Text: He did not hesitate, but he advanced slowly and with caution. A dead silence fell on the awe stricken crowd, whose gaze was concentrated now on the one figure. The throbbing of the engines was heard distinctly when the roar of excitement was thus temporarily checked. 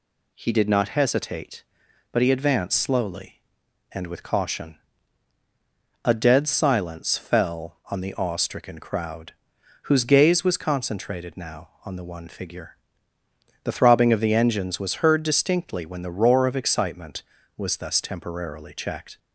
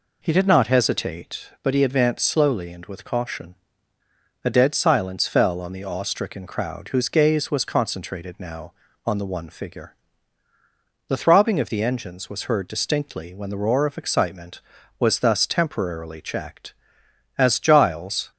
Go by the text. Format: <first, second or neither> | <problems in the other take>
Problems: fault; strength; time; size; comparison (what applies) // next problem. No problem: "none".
first | goes on to say "As Giles"; noticeable; from 17.3 s on; 0.94 s long